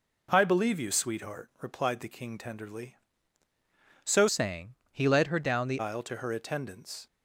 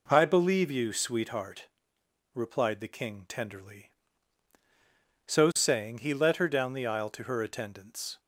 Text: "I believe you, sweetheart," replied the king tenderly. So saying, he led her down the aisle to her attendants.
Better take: second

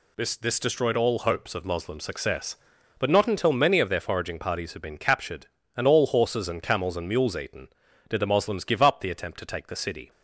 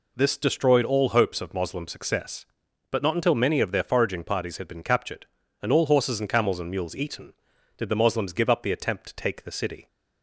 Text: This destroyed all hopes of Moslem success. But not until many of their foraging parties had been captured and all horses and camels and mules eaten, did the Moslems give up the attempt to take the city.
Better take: second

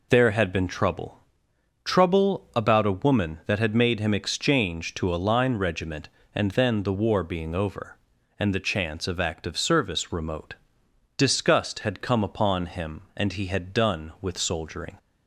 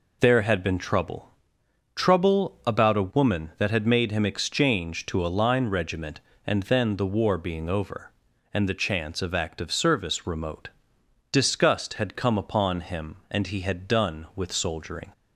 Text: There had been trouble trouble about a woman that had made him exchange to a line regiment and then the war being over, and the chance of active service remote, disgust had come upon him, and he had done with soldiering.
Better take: neither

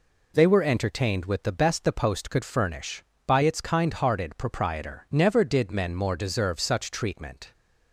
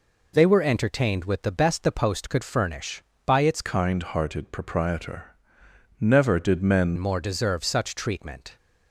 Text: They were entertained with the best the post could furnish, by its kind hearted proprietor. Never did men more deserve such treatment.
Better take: first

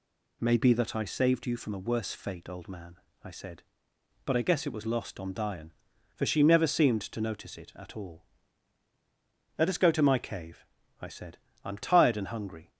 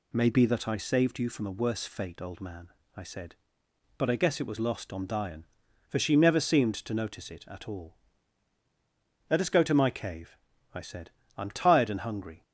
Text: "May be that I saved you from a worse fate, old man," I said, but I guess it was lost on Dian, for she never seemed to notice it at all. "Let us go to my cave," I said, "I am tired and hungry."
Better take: neither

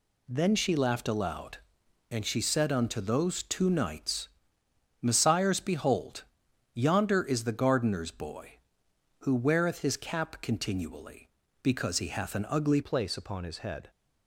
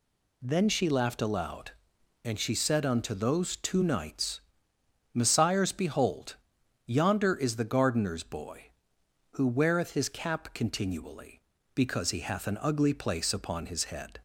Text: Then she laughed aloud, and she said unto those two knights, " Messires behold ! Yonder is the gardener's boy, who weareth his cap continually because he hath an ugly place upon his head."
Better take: second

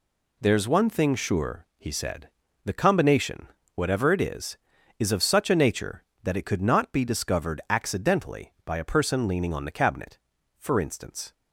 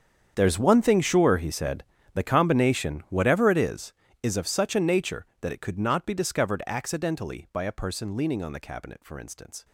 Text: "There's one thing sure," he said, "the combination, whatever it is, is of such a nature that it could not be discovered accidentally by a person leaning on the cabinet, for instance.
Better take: first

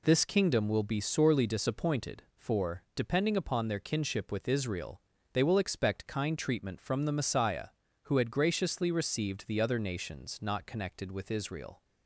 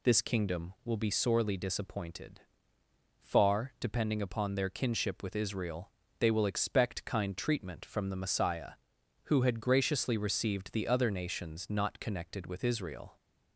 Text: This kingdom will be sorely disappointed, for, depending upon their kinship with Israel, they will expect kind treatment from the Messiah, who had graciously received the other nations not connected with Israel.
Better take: first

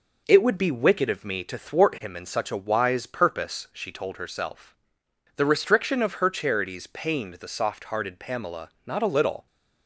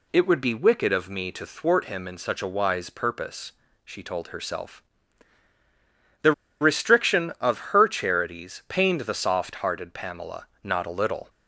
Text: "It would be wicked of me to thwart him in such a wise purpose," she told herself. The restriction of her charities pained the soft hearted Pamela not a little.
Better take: first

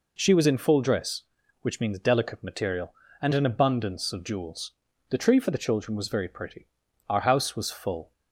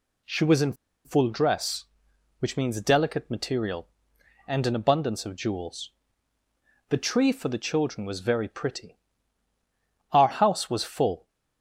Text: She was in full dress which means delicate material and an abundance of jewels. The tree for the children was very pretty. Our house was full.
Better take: first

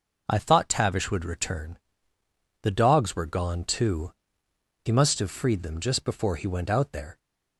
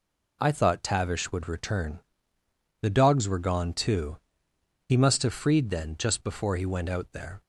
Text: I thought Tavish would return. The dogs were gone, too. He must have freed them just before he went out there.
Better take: first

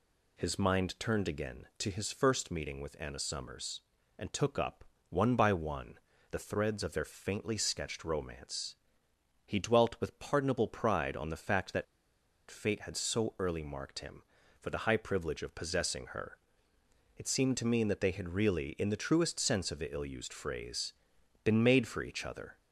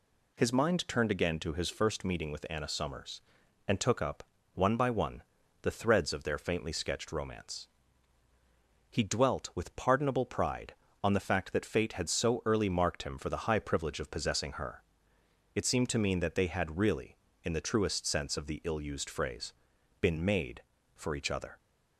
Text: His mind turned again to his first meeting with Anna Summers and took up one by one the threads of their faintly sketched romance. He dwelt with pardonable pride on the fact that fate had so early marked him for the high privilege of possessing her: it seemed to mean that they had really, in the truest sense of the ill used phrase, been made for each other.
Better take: second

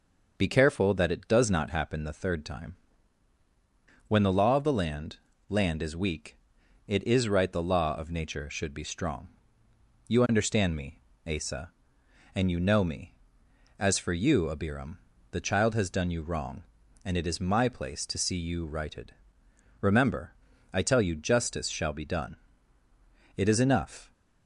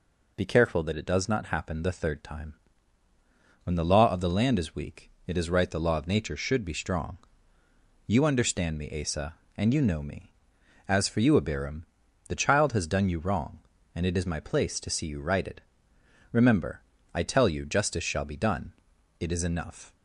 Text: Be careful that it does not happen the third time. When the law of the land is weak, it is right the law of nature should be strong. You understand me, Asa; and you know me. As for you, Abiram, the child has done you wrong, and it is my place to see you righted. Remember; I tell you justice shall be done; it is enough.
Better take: second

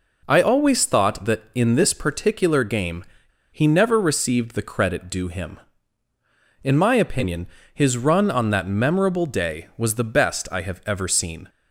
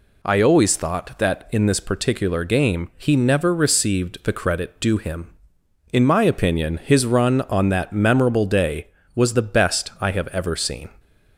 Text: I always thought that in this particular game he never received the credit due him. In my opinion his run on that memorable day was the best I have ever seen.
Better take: second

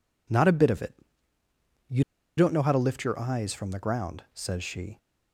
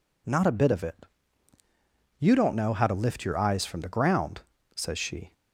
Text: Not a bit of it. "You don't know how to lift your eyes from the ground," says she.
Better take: second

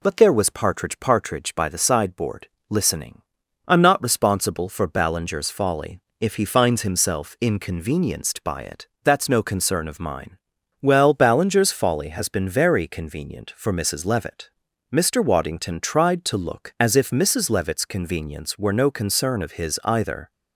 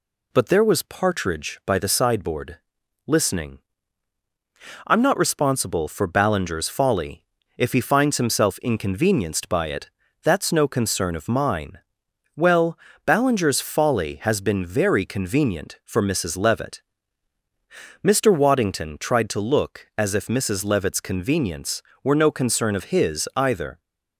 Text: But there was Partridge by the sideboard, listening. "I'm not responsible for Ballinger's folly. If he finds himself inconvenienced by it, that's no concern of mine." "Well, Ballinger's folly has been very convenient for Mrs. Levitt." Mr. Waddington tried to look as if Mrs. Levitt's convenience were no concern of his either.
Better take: second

